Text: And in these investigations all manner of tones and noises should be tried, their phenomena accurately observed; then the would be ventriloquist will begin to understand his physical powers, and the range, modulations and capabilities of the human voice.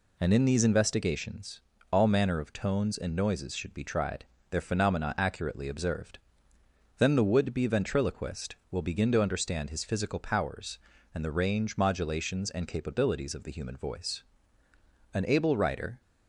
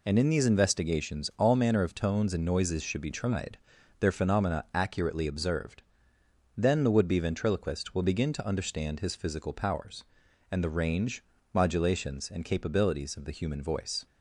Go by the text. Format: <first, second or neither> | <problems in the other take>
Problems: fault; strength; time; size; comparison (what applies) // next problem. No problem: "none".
second | pauses between "investigations" and "all"; slight; at 1.6 s; 0.32 s long // goes on to say "An able writer"; noticeable; from 15.1 s on; 0.88 s long